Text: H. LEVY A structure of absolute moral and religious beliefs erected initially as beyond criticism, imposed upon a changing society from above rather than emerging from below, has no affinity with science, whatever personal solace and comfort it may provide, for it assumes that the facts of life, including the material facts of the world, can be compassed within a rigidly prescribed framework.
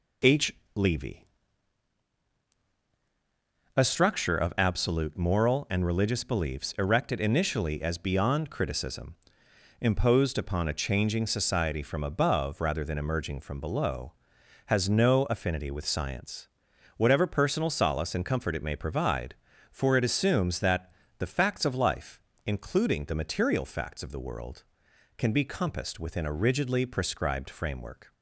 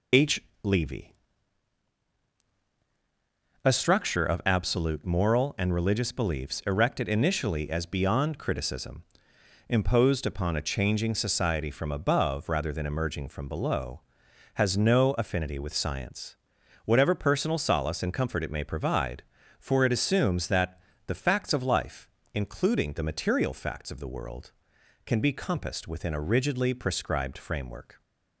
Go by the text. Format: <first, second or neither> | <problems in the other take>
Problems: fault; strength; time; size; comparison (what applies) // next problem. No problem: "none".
first | loses the start of "H"; at 0.1 s; 25 ms // pauses between "LEVY" and "A"; strong; at 1.1 s; 2.5 s long; strong in the first // pauses between "that" and "the"; slight; at 20.8 s; 0.26 s long; slight in the first